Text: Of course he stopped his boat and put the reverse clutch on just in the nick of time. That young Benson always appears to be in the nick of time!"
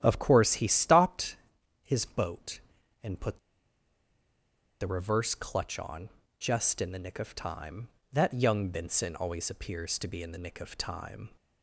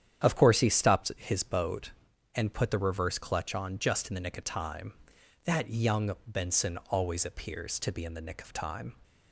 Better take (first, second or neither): second